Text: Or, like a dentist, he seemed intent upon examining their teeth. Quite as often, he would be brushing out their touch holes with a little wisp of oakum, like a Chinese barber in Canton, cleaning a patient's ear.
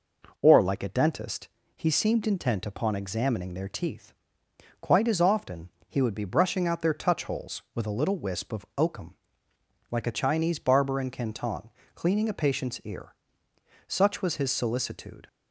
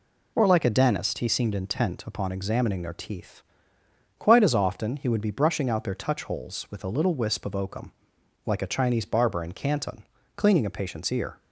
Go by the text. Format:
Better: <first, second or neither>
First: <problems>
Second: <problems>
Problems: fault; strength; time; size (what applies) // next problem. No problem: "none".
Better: second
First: goes on to say "Such was his solicitude"; from 13.8 s on; 1.4 s long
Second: none